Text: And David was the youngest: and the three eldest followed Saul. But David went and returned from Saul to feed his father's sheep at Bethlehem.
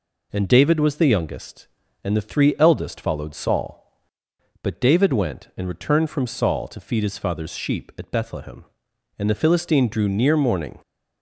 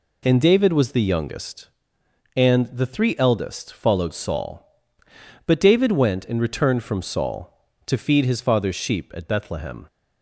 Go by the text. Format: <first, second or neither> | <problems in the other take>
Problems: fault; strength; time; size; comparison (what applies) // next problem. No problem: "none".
second | goes on to say "And the Philistine drew near morning"; from 9.1 s on; 1.6 s long